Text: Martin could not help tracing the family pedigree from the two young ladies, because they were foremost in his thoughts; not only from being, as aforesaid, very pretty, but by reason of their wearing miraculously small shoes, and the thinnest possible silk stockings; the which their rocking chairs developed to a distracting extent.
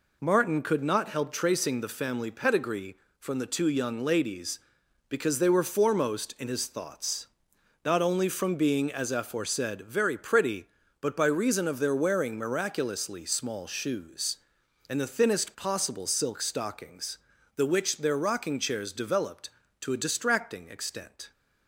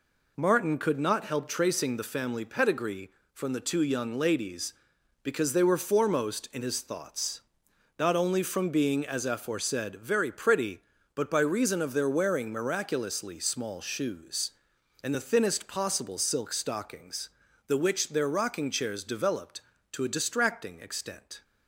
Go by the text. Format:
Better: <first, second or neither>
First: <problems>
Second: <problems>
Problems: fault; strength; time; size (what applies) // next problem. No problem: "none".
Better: neither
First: none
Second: none